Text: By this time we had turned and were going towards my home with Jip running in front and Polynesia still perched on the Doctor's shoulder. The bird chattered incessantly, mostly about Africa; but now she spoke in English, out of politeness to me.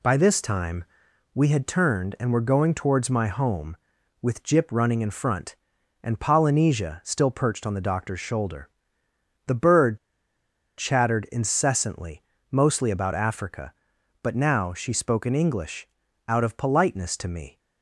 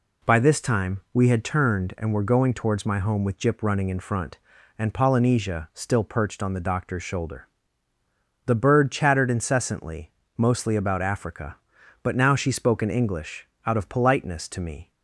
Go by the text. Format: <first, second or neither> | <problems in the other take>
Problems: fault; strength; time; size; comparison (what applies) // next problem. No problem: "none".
second | pauses between "time" and "we"; noticeable; at 0.8 s; 0.50 s long // pauses between "bird" and "chattered"; noticeable; at 9.9 s; 0.80 s long